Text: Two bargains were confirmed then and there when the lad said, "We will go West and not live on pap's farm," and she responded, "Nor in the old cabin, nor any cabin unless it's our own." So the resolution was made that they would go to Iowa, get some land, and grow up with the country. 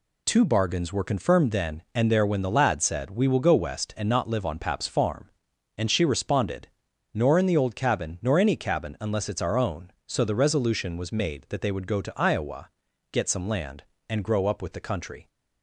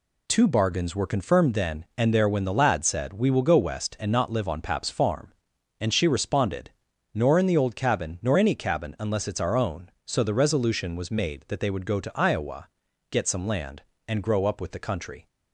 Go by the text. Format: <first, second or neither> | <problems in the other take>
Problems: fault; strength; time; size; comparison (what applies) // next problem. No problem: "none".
neither | none